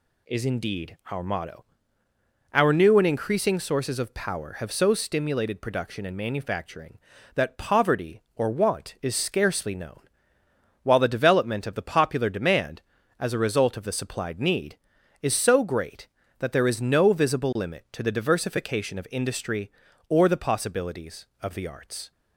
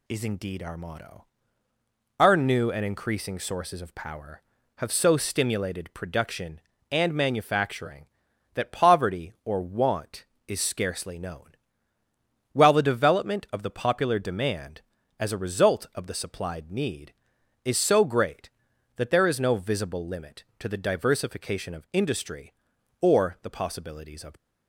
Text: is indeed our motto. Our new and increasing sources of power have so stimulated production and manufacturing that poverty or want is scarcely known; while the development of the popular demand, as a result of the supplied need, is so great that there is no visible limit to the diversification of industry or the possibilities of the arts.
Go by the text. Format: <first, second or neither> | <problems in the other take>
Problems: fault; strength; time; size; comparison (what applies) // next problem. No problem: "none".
first | stops before "the arts"; at 24.3 s